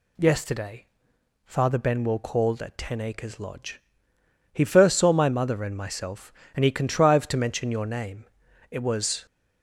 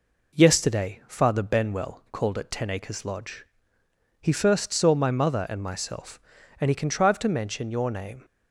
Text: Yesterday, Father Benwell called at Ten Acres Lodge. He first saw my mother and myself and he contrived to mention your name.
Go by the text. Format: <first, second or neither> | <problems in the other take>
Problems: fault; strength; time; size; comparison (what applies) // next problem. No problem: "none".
second | goes on to say "It was"; from 8.6 s on; 0.56 s long